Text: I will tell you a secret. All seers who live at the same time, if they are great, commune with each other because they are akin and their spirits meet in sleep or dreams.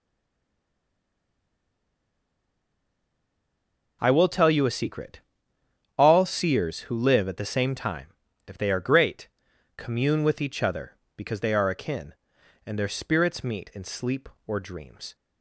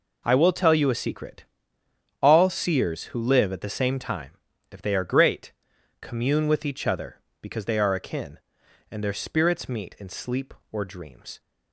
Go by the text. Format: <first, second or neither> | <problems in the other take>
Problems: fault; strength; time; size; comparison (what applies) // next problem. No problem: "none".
second | stays silent before the first word; strong; until 4.0 s; 4.0 s long